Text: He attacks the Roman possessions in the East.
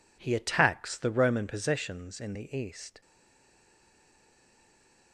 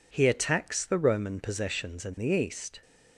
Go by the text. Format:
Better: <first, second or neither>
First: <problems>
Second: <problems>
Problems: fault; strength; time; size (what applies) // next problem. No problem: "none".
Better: second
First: stays silent after the last word; from 3.0 s on; 2.1 s long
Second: none